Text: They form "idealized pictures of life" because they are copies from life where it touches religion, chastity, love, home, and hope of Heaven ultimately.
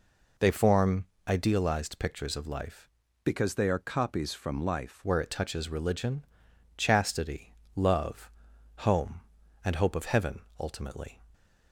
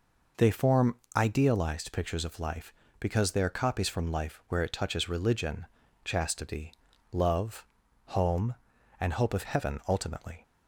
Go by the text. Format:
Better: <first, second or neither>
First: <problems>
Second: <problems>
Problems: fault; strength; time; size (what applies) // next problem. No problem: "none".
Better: second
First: pauses between "form" and "idealized"; slight; at 1.0 s; 0.22 s long // changes voice from "because" to "life"; from 3.2 to 5.0 s; 1.8 s long // pauses between "Heaven" and "ultimately"; slight; at 10.4 s; 0.18 s long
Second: pauses between "form" and "idealized"; slight; at 0.9 s; 0.18 s long